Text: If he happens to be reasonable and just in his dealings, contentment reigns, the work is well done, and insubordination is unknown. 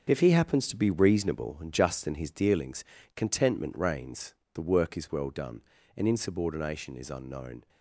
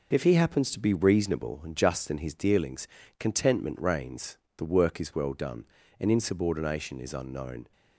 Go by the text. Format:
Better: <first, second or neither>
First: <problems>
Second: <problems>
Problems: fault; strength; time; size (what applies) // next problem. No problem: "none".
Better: second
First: gets quieter; strong; throughout; 9 dB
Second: none